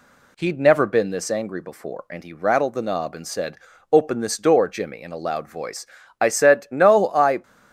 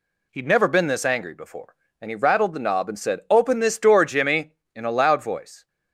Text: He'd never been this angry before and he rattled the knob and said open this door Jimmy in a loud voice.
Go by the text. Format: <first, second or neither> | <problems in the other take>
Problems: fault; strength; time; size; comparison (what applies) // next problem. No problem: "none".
second | pauses between "said" and "open"; slight; at 3.5 s; 0.34 s long // goes on to say "I said no I"; noticeable; from 6.2 s on; 1.2 s long